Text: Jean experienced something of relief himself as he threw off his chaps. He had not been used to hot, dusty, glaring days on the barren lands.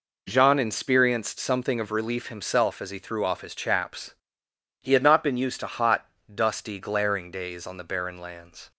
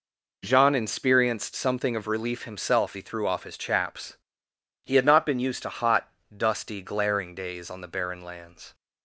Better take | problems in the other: first | skips "as"; at 2.9 s

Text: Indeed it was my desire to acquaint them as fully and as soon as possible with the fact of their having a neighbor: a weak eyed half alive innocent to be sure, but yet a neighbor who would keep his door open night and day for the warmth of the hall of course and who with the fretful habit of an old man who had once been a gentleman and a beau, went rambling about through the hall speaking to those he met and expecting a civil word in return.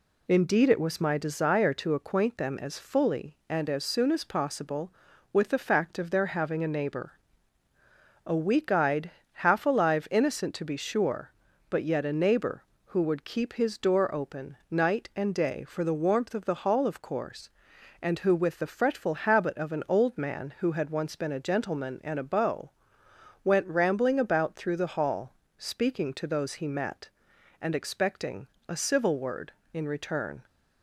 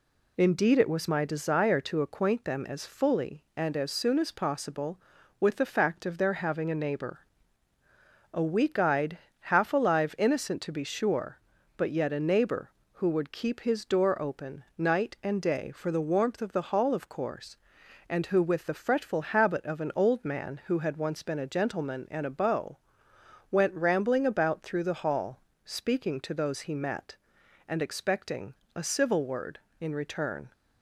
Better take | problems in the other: neither | pauses between "eyed" and "half"; slight; the same in both // pauses between "hall" and "speaking"; slight; the same in both // pauses between "expecting" and "a"; slight; the same in both

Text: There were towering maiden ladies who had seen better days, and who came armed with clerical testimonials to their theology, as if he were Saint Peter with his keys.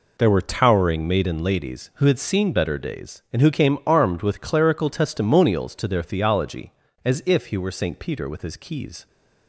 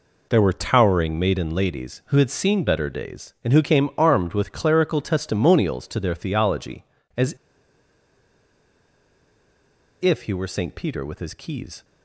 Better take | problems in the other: first | pauses between "as" and "if"; strong; at 7.3 s; 2.6 s long

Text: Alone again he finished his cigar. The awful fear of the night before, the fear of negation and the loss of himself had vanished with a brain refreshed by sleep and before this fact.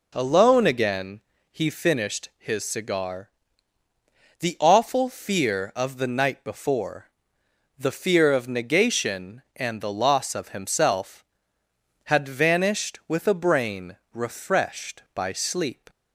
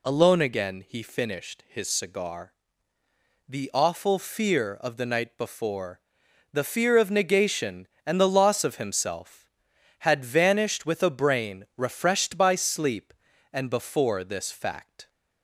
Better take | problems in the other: second | pauses between "again" and "he"; slight; at 1.2 s; 0.30 s long // pauses between "brain" and "refreshed"; slight; at 13.9 s; 0.18 s long // stops before "and before this fact"; at 15.8 s

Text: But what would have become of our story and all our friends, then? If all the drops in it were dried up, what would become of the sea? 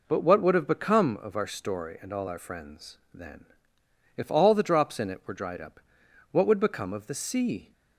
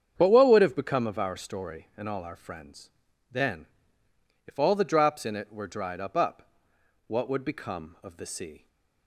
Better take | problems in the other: first | starts louder than the rest; strong; until 1.1 s; 8 dB // says "up" twice; at 6.1 s

